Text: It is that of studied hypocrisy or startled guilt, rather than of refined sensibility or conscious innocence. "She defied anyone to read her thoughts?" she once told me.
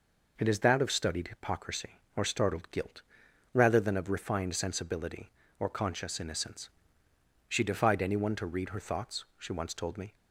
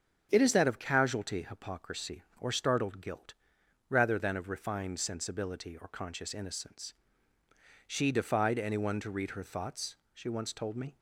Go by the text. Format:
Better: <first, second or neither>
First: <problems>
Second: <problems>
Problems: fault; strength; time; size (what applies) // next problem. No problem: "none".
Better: first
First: none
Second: starts louder than the rest; strong; until 1.3 s; 8 dB // says "casualty" for "studied"; at 0.7 s